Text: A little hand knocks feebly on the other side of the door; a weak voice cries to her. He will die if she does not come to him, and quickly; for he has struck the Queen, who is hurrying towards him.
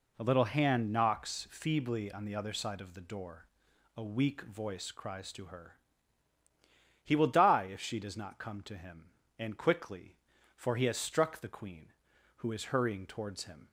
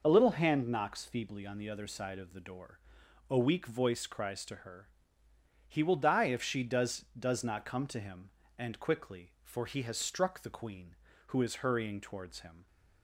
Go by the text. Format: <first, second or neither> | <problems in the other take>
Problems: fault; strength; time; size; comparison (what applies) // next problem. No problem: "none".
first | says "does" twice; at 7.1 s